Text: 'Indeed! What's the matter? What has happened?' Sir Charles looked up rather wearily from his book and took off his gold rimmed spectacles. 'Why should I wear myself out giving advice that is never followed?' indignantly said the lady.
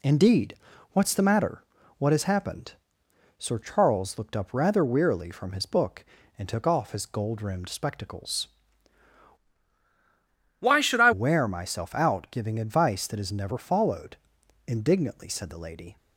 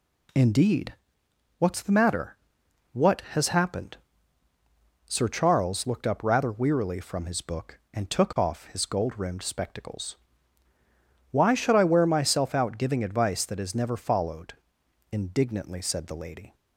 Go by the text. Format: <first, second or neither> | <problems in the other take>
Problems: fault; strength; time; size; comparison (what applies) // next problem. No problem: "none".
second | changes voice from "Why" to "I"; from 10.5 to 11.1 s; 0.6 s long